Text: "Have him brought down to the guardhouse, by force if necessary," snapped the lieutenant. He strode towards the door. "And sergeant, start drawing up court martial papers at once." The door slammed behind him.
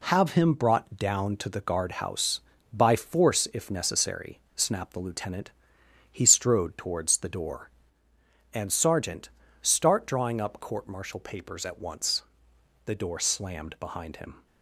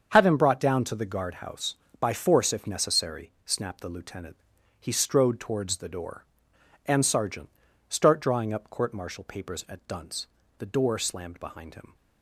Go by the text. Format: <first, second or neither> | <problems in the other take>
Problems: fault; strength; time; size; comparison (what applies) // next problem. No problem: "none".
first | starts louder than the rest; until 1.1 s; 7 dB // says "dunce" for "once"; at 9.8 s